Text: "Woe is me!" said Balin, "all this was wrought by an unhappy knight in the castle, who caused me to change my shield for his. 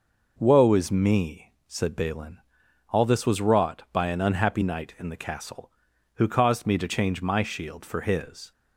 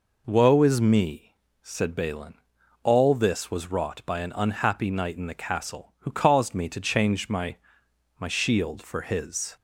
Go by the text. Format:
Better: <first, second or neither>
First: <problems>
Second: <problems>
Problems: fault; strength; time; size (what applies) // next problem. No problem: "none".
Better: first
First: none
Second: says "my" twice; at 8.1 s